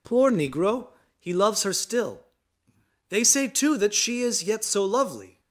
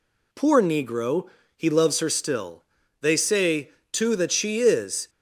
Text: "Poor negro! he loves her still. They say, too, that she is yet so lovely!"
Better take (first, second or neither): first